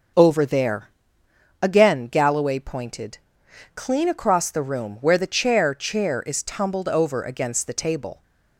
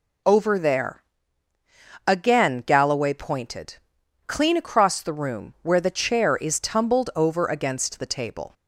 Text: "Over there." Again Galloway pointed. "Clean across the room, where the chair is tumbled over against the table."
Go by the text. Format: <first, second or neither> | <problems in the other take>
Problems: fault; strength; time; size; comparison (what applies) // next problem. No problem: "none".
second | starts louder than the rest; until 1.8 s; 6.5 dB // says "chair" twice; at 5.7 s